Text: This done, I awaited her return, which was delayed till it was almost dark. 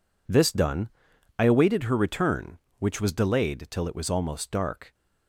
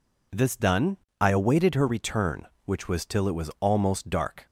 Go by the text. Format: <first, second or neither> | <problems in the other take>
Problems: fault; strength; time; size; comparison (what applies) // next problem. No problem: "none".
first | skips "delayed"; at 3.0 s